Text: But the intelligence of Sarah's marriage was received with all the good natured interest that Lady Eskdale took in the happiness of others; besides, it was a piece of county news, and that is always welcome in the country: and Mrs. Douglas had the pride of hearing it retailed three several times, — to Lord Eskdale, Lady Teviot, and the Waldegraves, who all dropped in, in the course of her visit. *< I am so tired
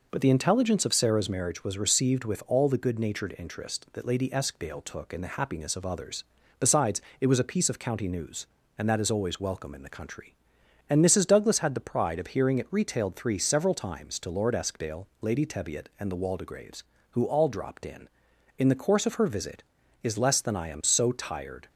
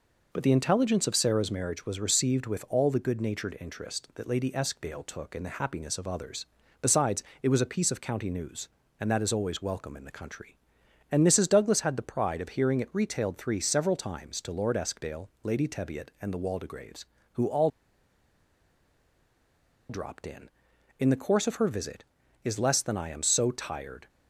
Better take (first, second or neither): first